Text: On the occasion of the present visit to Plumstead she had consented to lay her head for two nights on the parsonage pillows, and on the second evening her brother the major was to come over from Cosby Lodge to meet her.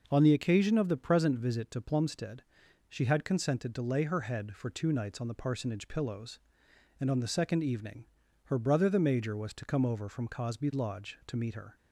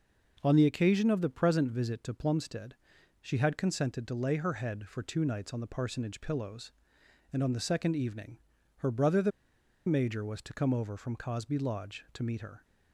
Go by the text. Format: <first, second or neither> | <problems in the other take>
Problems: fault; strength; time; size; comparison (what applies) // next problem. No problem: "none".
first | pauses between "Plumstead" and "she"; at 2.7 s; 0.44 s long; also in the first // pauses between "evening" and "her"; at 8.3 s; 0.38 s long; also in the first // pauses between "the" and "major"; noticeable; at 9.3 s; 0.57 s long